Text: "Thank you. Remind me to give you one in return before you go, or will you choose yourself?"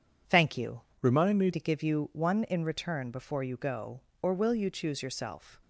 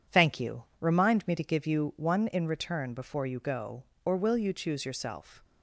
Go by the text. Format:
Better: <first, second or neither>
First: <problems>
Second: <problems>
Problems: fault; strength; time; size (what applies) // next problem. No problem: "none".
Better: second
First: changes voice from "Remind" to "me"; from 1.0 to 1.5 s; 0.5 s long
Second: none